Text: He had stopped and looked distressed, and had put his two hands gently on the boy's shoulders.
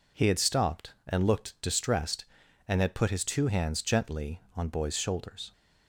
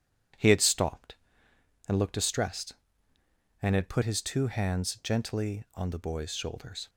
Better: second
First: skips "the"; at 4.6 s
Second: none

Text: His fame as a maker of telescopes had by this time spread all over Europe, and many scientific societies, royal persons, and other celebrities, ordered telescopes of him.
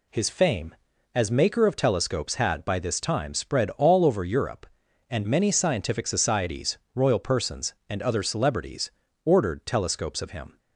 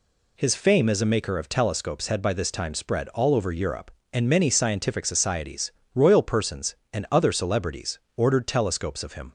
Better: second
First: skips "a"; at 1.2 s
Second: none

